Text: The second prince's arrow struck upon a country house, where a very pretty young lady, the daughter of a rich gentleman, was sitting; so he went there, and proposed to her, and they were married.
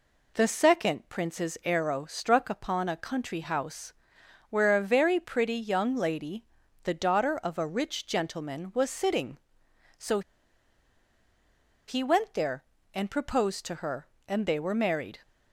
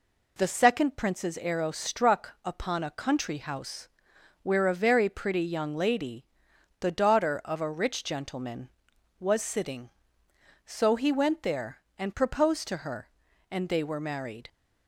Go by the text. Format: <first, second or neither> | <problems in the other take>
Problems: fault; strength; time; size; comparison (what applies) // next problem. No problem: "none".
second | pauses between "so" and "he"; strong; at 10.2 s; 1.6 s long